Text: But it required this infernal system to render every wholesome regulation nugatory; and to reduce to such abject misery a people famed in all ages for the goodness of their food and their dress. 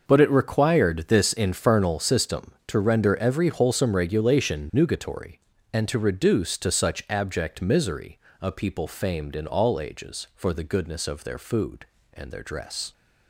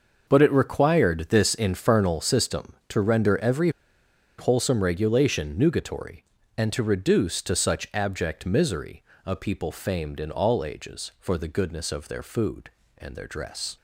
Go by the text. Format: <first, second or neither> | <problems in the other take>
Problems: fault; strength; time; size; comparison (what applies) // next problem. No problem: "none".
first | pauses between "every" and "wholesome"; noticeable; at 3.7 s; 0.68 s long // pauses between "misery" and "a"; slight; at 9.0 s; 0.24 s long; slight in the first